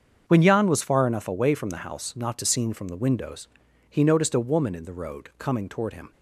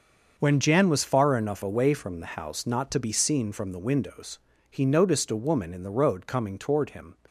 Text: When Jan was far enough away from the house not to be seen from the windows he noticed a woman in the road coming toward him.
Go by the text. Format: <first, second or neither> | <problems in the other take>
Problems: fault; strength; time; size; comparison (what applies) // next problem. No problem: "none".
second | starts louder than the rest; strong; until 1.2 s; 7 dB; also in the second // skips "be"; at 2.4 s // pauses between "windows" and "he"; at 3.4 s; 0.42 s long; slight in the second